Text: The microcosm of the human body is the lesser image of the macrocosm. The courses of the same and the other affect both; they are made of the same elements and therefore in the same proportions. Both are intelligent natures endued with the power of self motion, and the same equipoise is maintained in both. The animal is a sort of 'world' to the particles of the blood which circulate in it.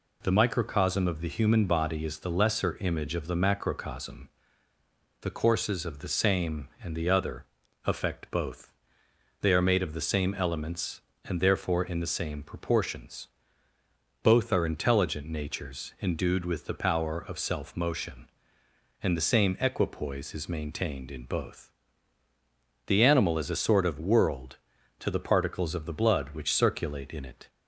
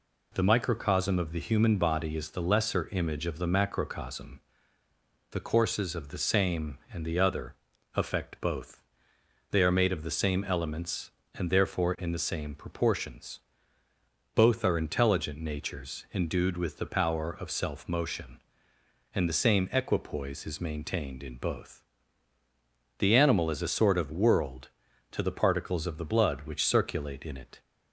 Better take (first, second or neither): neither